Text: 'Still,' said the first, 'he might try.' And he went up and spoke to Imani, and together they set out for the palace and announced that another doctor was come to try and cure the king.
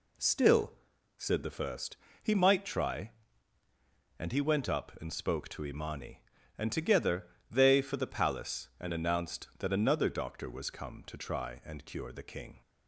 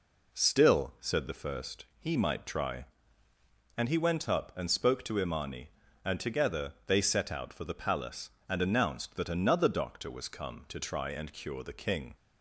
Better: second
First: pauses between "together" and "they"; slight; at 7.2 s; 0.24 s long // skips "set out"; at 7.8 s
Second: none

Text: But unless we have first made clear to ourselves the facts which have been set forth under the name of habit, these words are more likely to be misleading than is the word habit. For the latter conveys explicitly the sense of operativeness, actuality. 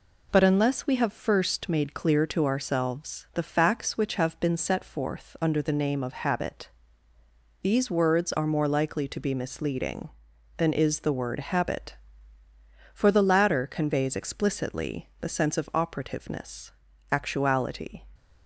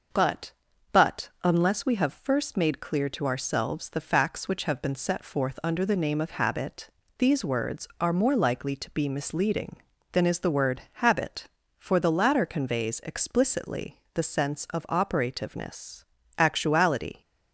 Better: first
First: none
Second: starts louder than the rest; noticeable; until 1.6 s; 6 dB // says "But" twice; at 0.9 s

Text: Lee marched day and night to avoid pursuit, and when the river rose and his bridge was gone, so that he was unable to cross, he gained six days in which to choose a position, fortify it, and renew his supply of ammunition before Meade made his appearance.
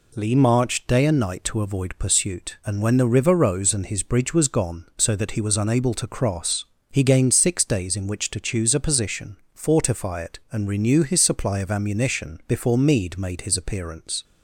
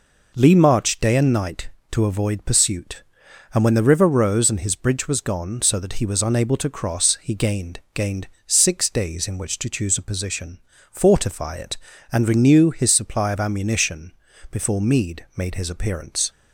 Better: first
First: none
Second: says "gained" twice; at 7.9 s // pauses between "ammunition" and "before"; at 14.1 s; 0.40 s long

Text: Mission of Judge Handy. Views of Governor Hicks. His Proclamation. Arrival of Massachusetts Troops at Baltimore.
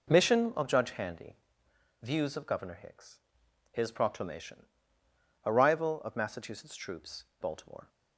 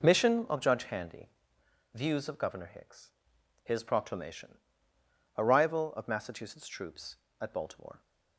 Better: second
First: skips "at"; at 7.3 s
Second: none

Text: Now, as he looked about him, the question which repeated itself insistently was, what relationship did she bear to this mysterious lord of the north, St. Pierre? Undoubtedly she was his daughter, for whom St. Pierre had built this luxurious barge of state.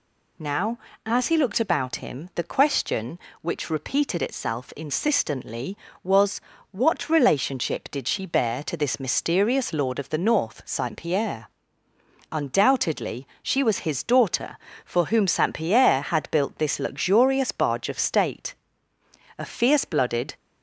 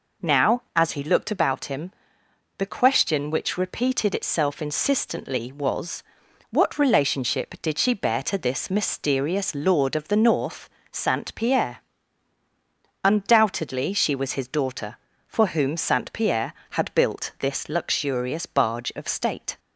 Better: second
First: pauses between "Undoubtedly" and "she"; slight; at 13.2 s; 0.16 s long // goes on to say "A fierce blooded"; noticeable; from 19.3 s on; 0.98 s long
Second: none

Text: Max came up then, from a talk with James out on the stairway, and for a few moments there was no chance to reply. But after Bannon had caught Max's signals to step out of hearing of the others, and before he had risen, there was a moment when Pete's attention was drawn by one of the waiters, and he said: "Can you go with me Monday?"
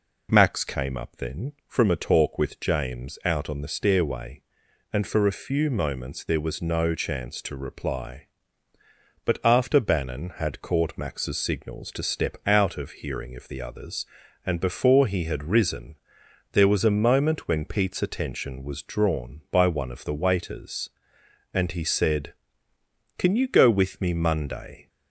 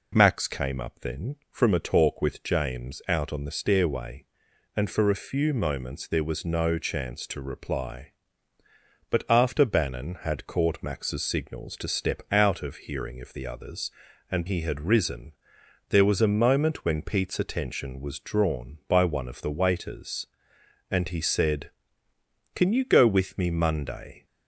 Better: first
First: none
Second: skips "before"; at 14.4 s

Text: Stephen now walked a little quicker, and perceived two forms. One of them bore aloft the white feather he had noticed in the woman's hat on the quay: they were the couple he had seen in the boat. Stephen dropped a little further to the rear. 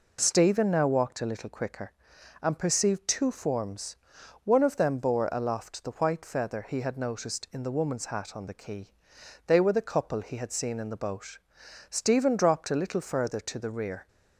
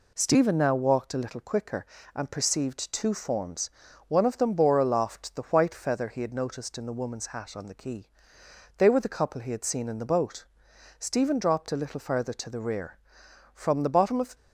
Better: first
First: none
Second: goes on to say "From the bottom of"; noticeable; from 13.5 s on; 0.80 s long

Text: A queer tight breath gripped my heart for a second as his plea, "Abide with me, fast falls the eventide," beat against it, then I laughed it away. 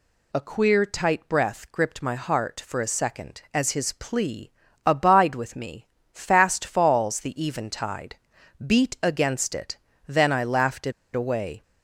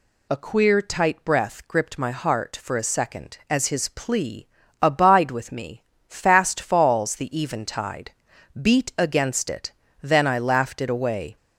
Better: second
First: pauses between "it" and "away"; slight; at 10.9 s; 0.21 s long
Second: none

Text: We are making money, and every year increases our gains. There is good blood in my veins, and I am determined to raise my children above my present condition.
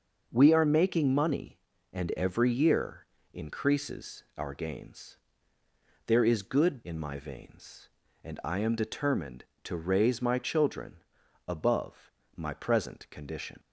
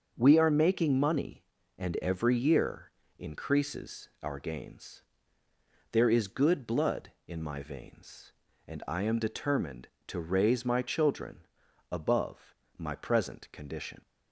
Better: second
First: starts louder than the rest; until 1.3 s; 6.5 dB // pauses between "year" and "increases"; slight; at 3.0 s; 0.26 s long // skips "blood"; at 6.8 s // pauses between "children" and "above"; noticeable; at 10.9 s; 0.50 s long // pauses between "above" and "my"; slight; at 12.0 s; 0.26 s long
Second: starts louder than the rest; until 1.1 s; 6.5 dB // pauses between "year" and "increases"; slight; at 2.9 s; 0.26 s long // pauses between "children" and "above"; noticeable; at 11.3 s; 0.50 s long // pauses between "above" and "my"; slight; at 12.5 s; 0.24 s long

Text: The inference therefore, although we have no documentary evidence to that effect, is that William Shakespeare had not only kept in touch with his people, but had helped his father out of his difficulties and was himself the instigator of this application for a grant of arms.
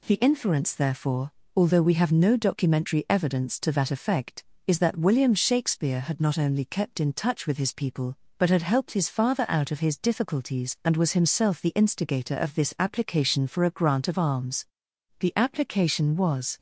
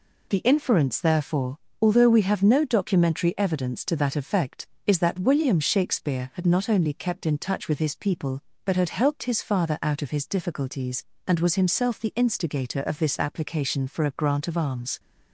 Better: second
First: goes on to say "The application was"; from 15.1 s on; 1.3 s long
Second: none

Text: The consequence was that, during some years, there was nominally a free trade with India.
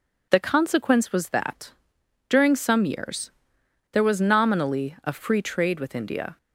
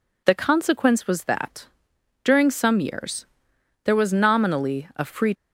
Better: first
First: none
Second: stops before "trade with India"; at 5.3 s

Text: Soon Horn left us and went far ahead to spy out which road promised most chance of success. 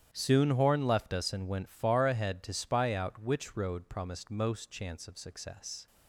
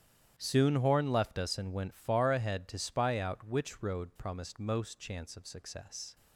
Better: neither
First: starts louder than the rest; strong; until 1.1 s; 10 dB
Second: starts louder than the rest; strong; until 1.3 s; 10 dB

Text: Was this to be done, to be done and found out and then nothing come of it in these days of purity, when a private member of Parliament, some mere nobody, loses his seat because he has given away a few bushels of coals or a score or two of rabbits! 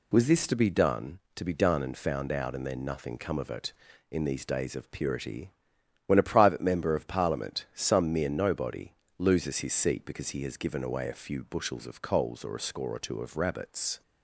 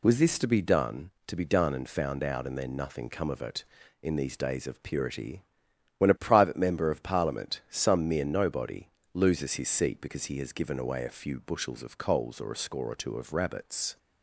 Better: neither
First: none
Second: none

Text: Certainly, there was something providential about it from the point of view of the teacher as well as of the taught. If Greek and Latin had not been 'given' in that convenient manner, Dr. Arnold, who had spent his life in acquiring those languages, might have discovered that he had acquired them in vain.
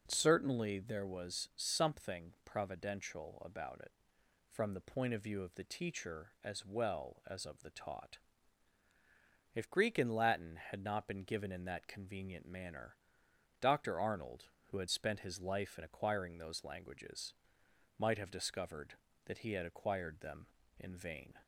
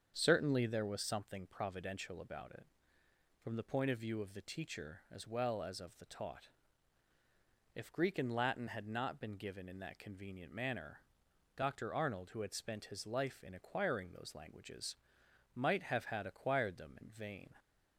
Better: first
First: none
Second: starts louder than the rest; strong; until 1.1 s; 7.5 dB // skips "discovered that he"; at 16.0 s

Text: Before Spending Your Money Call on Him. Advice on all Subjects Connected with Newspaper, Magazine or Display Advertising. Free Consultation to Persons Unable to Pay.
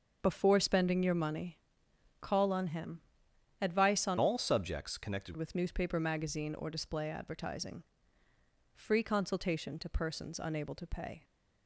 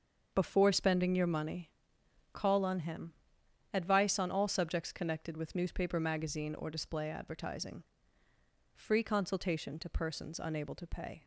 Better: second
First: starts louder than the rest; until 1.2 s; 6.5 dB // pauses between "Money" and "Call"; noticeable; at 1.5 s; 0.60 s long // changes voice from "all" to "Connected"; from 4.1 to 5.3 s; 1.2 s long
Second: starts louder than the rest; until 1.3 s; 6.5 dB // pauses between "Money" and "Call"; noticeable; at 1.7 s; 0.60 s long

